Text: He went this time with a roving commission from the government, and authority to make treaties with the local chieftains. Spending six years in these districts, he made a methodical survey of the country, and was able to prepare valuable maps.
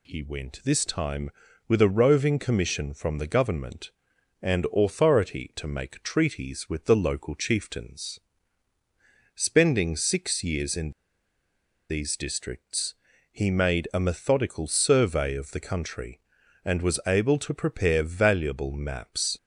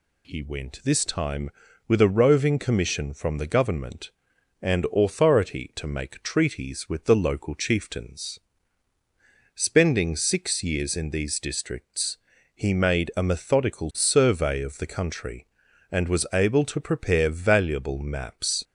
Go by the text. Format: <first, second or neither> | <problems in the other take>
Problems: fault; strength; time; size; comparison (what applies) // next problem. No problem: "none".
second | pauses between "in" and "these"; noticeable; at 10.9 s; 0.97 s long